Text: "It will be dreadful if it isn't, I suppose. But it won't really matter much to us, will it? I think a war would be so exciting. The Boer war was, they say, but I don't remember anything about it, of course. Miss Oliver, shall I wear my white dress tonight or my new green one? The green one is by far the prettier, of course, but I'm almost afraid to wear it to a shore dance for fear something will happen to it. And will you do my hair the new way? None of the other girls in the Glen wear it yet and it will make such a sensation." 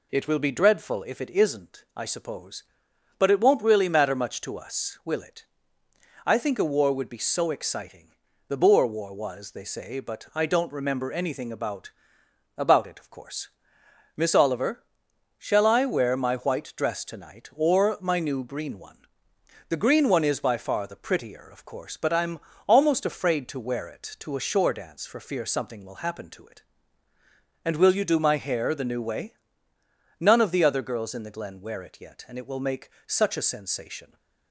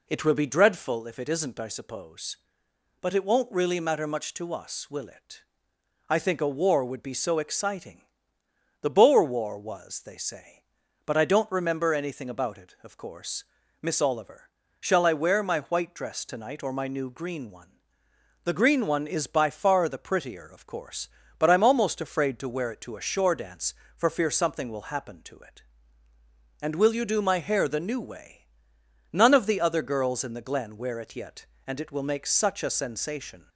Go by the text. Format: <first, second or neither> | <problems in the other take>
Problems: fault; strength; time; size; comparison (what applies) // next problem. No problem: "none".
second | says "about" twice; at 12.5 s // pauses between "I'm" and "almost"; slight; at 22.3 s; 0.28 s long // pauses between "make" and "such"; slight; at 32.9 s; 0.16 s long